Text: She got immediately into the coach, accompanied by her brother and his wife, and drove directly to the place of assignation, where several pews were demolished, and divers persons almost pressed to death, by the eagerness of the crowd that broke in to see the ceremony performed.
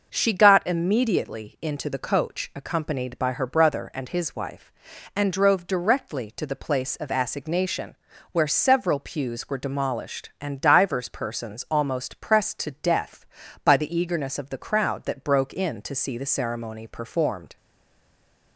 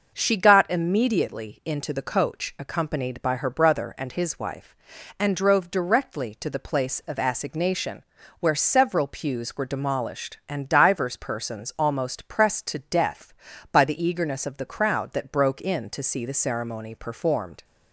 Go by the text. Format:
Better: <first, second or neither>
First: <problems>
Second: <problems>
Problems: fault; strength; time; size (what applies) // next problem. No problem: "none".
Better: second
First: stays silent after the last word; from 17.5 s on; 1.0 s long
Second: none